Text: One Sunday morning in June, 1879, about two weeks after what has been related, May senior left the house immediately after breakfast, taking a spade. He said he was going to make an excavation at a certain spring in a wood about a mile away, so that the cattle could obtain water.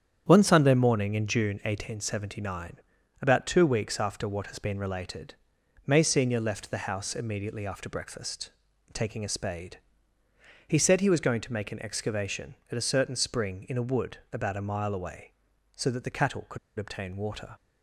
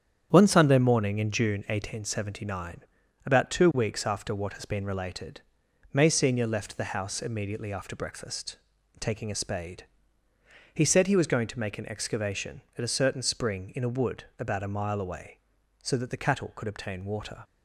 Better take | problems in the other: second | starts louder than the rest; strong; until 1.2 s; 8.5 dB; strong in the second // pauses between "wood" and "about"; slight; at 14.1 s; 0.16 s long; slight in the second // pauses between "could" and "obtain"; slight; at 16.5 s; 0.20 s long

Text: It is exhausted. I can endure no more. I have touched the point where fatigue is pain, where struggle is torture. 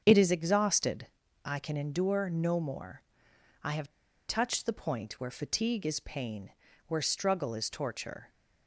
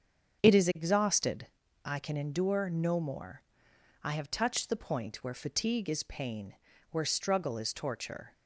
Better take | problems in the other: second | starts louder than the rest; strong; until 1.0 s; 7.5 dB; strong in the second // pauses between "have" and "touched"; at 3.8 s; 0.39 s long

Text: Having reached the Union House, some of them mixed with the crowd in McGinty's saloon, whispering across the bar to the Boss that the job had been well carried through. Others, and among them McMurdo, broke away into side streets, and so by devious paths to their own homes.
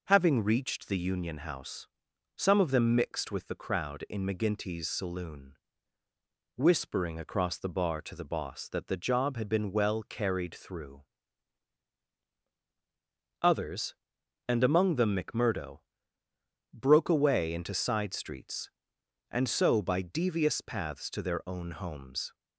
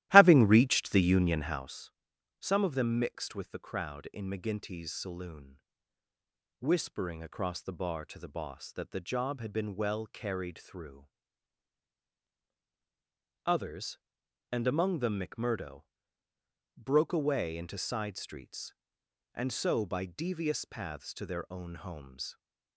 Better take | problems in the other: first | starts louder than the rest; strong; until 1.8 s; 15.5 dB

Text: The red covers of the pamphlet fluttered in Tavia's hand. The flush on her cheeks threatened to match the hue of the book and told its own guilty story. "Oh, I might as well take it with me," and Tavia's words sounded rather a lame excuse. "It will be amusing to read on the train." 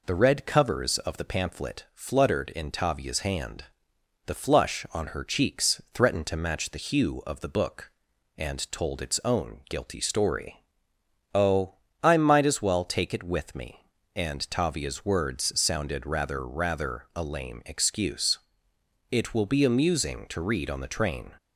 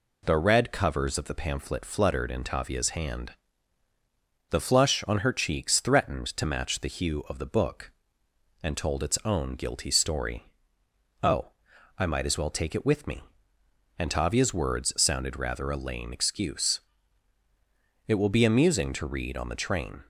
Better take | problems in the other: second | says "rather" twice; at 16.4 s

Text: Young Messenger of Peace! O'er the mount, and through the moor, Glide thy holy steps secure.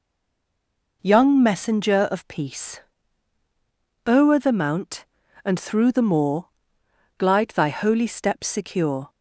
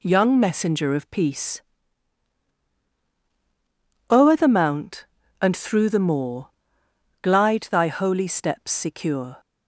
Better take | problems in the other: second | stays silent before the first word; until 1.0 s; 1.0 s long

